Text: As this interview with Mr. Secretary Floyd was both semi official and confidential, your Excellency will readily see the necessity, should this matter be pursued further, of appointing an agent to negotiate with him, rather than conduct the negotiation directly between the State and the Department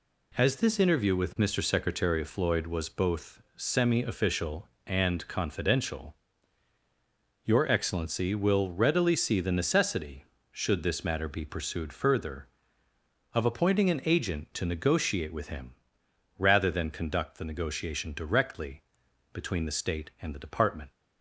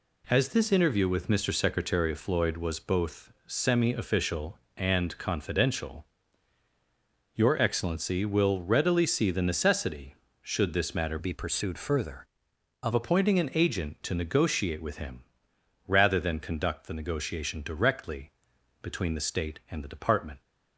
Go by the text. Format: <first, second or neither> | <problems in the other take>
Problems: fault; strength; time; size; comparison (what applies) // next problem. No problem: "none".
first | changes voice from "be" to "of"; from 11.1 to 12.9 s; 1.8 s long // pauses between "directly" and "between"; noticeable; at 18.2 s; 0.50 s long; noticeable in the first